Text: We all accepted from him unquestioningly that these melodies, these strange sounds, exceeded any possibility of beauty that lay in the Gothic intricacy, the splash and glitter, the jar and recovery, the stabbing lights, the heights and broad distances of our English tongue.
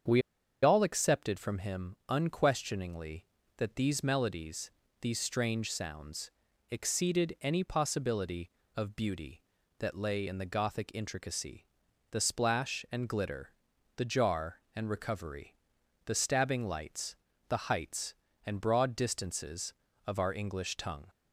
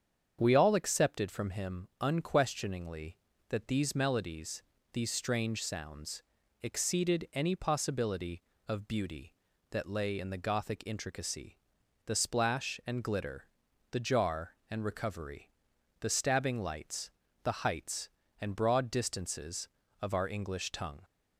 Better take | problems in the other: second | starts louder than the rest; strong; until 1.5 s; 7.5 dB; strong in the second // pauses between "We" and "all"; at 0.2 s; 0.42 s long

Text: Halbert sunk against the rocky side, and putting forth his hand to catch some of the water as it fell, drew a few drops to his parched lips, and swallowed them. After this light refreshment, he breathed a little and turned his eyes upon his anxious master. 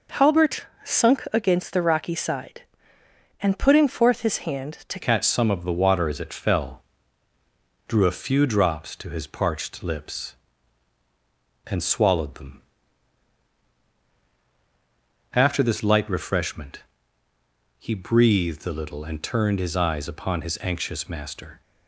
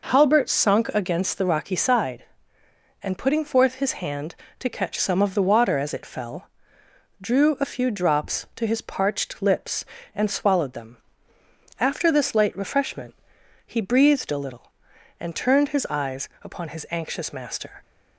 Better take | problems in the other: second | pauses between "Halbert" and "sunk"; slight; at 0.6 s; 0.16 s long // changes voice at "catch"; from 5.0 s on; 16.6 s long

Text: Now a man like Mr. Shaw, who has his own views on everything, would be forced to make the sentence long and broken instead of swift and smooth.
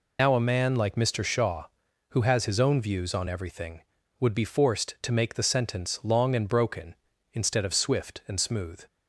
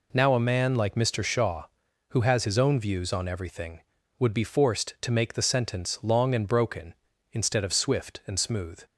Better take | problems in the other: second | loses the start of "Now"; at 0.1 s; 90 ms

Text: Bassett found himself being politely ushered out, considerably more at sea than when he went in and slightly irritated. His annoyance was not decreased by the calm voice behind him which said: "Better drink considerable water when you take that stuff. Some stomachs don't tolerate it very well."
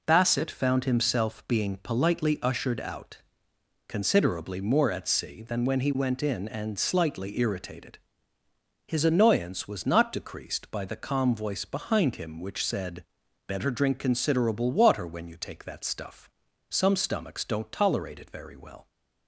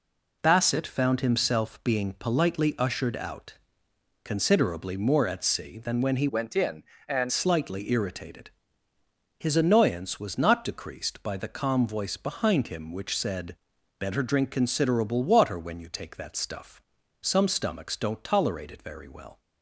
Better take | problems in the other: first | changes voice from "went" to "and"; from 6.2 to 7.3 s; 1.1 s long

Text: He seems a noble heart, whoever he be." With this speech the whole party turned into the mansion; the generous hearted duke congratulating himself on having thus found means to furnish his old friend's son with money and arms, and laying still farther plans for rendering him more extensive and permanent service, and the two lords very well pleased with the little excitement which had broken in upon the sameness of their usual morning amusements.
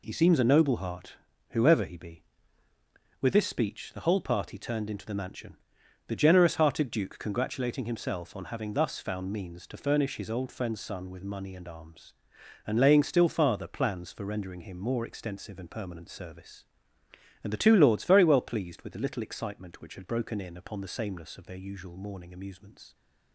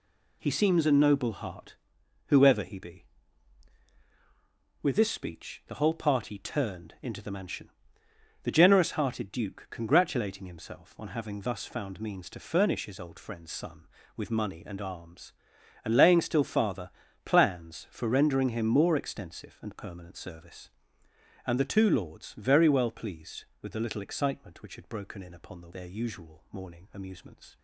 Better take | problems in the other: first | pauses between "farther" and "plans"; slight; at 16.8 s; 0.36 s long // skips "sameness of"; at 25.6 s

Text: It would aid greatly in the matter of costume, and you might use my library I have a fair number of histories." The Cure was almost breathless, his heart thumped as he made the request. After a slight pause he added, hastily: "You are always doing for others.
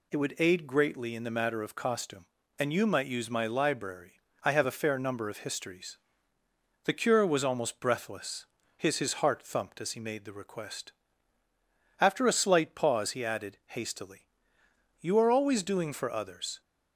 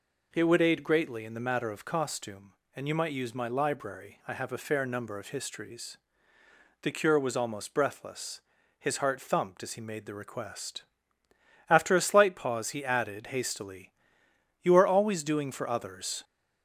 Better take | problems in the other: second | pauses between "library" and "I"; slight; at 4.1 s; 0.30 s long // says "his" twice; at 8.9 s

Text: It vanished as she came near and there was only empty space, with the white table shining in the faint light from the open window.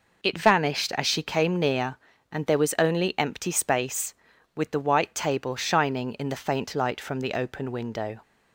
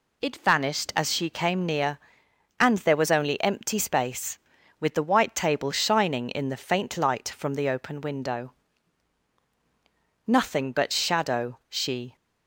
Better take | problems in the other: first | goes on to say "Nothing but shadow she"; strong; from 10.2 s on; 1.8 s long

